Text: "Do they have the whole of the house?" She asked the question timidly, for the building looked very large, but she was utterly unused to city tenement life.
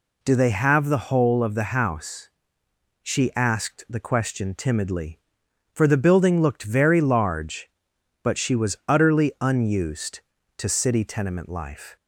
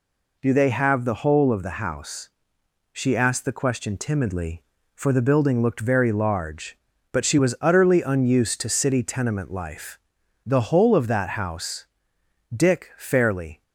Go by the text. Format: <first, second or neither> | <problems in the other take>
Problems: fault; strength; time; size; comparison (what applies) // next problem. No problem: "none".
first | goes on to say "The whole of that house Dick fairly"; strong; from 10.4 s on; 3.1 s long